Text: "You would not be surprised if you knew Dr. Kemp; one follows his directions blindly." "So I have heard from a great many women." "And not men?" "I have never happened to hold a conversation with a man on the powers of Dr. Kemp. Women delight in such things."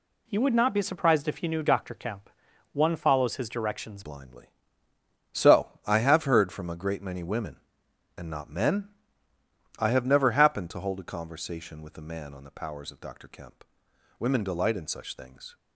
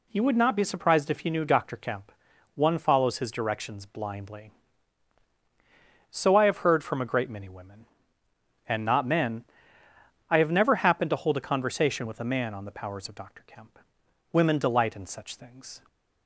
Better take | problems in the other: second | changes voice at "blindly"; from 4.0 s on; 11.5 s long

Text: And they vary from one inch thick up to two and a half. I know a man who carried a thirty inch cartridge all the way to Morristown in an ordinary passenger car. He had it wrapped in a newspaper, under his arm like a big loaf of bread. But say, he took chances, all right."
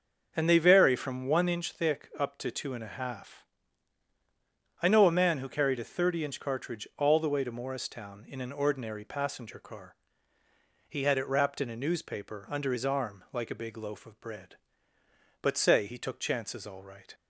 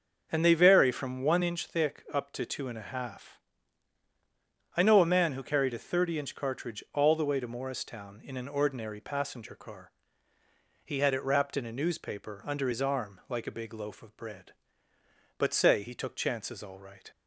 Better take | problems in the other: neither | starts louder than the rest; the same in both

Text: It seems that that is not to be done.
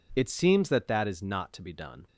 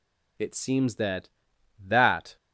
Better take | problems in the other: first | stops before "is not to be done"; at 2.3 s

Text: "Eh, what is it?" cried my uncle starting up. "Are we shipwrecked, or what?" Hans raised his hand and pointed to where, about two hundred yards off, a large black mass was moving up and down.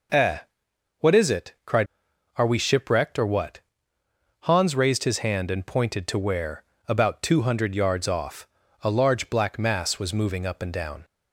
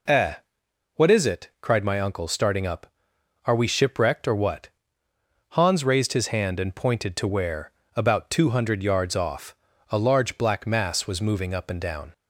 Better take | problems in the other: second | skips "my uncle starting up"; at 2.1 s

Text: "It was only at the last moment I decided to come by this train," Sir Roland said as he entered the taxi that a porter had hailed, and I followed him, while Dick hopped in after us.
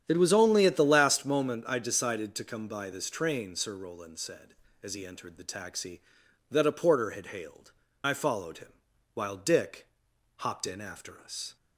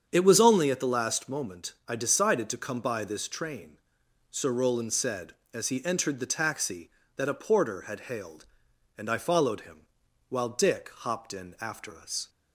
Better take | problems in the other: second | starts louder than the rest; strong; until 1.0 s; 9 dB; strong in the second // skips "and"; at 7.8 s // pauses between "Dick" and "hopped"; noticeable; at 9.8 s; 0.48 s long

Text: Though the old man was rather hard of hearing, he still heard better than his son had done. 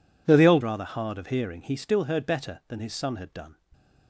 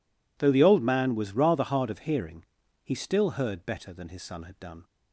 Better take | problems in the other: second | skips "man was"; at 0.6 s

